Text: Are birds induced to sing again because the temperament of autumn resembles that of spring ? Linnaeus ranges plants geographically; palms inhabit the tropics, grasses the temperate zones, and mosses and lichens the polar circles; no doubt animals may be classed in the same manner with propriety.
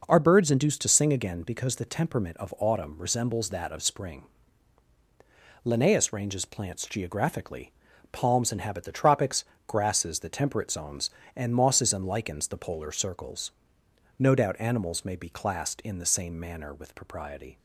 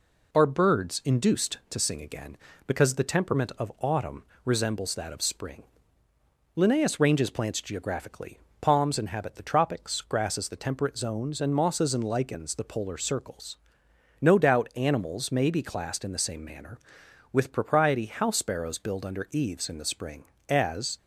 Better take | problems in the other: first | pauses between "autumn" and "resembles"; slight; at 4.2 s; 0.22 s long // goes on to say "House sparrows build under eaves in the spring as"; strong; from 18.0 s on; 2.9 s long

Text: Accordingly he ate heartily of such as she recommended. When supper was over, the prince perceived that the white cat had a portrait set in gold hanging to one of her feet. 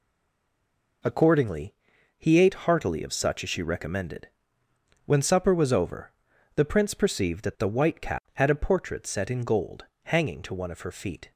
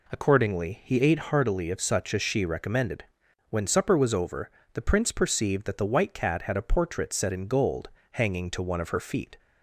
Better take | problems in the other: second | stays silent before the first word; until 1.0 s; 1.0 s long // pauses between "Accordingly" and "he"; at 1.7 s; 0.44 s long // pauses between "gold" and "hanging"; slight; at 9.8 s; 0.20 s long; slight in the second

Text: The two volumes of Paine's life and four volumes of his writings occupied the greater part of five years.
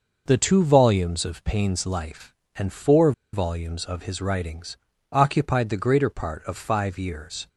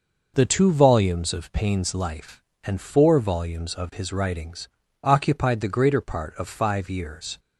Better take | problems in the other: second | pauses between "four" and "volumes"; slight; at 3.1 s; 0.20 s long // pauses between "writings" and "occupied"; slight; at 4.7 s; 0.34 s long; slight in the second

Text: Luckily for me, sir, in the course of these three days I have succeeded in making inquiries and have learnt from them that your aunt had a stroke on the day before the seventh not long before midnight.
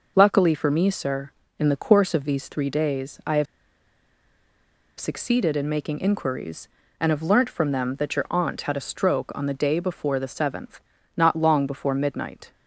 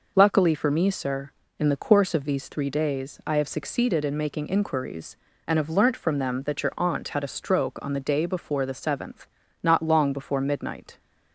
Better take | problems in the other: second | pauses between "have" and "succeeded"; strong; at 3.4 s; 1.5 s long // pauses between "seventh" and "not"; slight; at 10.8 s; 0.34 s long; slight in the second

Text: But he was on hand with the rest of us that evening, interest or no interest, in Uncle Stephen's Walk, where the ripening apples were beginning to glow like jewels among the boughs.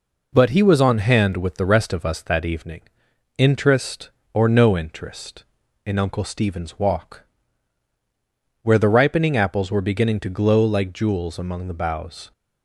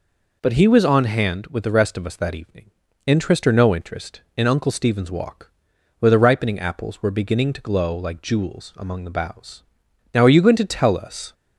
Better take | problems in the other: first | goes on to say "Now are you going to tell us"; noticeable; from 10.1 s on; 1.2 s long

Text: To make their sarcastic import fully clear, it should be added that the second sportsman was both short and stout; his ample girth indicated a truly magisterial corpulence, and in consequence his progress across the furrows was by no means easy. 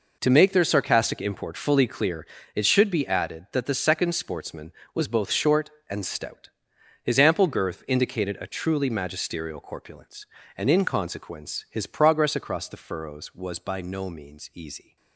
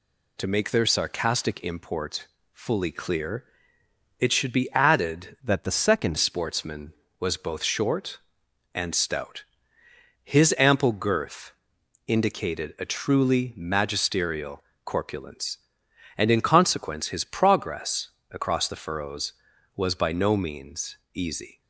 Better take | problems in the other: first | pauses between "import" and "fully"; slight; at 2.2 s; 0.24 s long // changes voice from "that" to "second"; from 5.4 to 6.1 s; 0.7 s long // pauses between "girth" and "indicated"; noticeable; at 11.5 s; 0.54 s long // pauses between "magisterial" and "corpulence"; slight; at 14.6 s; 0.24 s long // pauses between "progress" and "across"; slight; at 18.0 s; 0.22 s long // pauses between "means" and "easy"; slight; at 20.9 s; 0.18 s long

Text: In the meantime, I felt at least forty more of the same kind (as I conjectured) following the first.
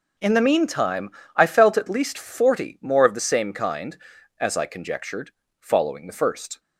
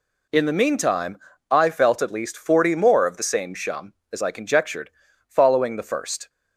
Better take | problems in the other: first | says "shum" for "kind"; at 3.5 s

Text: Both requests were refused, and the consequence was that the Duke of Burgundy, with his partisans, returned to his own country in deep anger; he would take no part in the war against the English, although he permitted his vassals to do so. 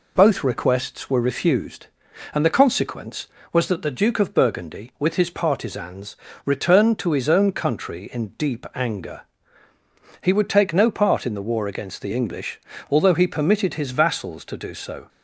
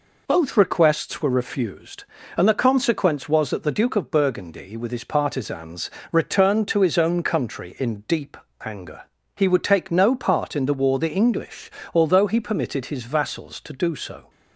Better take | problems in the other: first | pauses between "deep" and "anger"; slight; at 8.3 s; 0.26 s long // skips "against"; at 10.9 s

